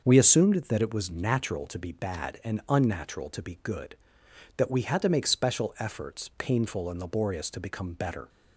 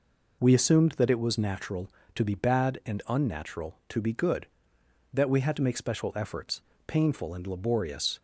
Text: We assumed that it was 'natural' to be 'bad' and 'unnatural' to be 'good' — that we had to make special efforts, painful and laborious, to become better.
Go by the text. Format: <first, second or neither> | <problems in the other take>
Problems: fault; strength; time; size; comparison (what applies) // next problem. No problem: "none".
first | stops before "to become better"; at 8.1 s